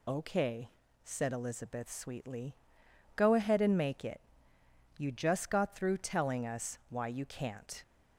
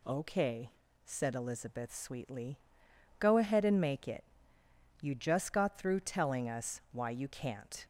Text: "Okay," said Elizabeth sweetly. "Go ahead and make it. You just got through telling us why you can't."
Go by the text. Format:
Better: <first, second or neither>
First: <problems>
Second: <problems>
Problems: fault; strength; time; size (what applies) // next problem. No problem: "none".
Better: second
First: loses the start of "Okay"; at 0.0 s; 40 ms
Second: none